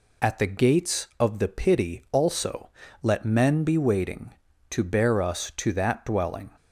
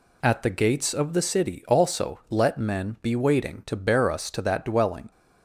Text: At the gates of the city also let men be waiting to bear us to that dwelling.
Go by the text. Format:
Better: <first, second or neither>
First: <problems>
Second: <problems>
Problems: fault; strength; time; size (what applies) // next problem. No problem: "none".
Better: second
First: says "pity" for "city"; at 1.4 s // pauses between "also" and "let"; slight; at 2.6 s; 0.32 s long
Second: none